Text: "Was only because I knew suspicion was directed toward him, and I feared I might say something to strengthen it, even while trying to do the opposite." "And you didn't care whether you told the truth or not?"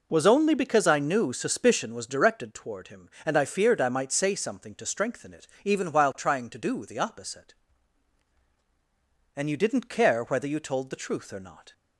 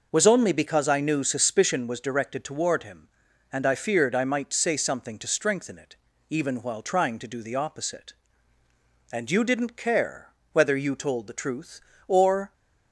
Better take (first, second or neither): first